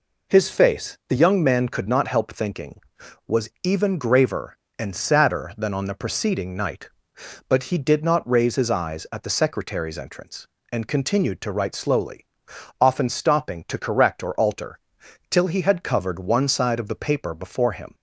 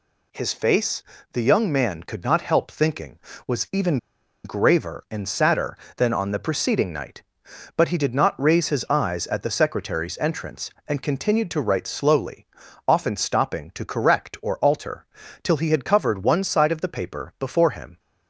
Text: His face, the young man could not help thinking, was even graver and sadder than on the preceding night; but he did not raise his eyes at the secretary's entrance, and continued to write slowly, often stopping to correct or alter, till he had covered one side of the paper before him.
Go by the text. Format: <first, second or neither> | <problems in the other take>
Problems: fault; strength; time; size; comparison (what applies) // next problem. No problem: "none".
first | pauses between "even" and "graver"; noticeable; at 3.9 s; 0.46 s long